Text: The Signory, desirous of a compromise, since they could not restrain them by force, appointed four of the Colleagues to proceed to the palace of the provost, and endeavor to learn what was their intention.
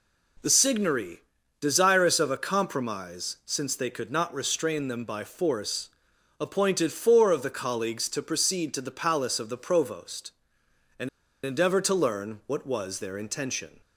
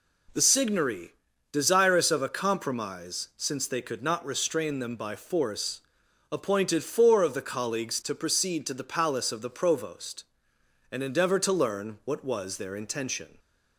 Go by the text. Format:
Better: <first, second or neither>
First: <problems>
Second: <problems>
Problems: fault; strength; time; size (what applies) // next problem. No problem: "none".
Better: second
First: pauses between "and" and "endeavor"; slight; at 11.0 s; 0.35 s long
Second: none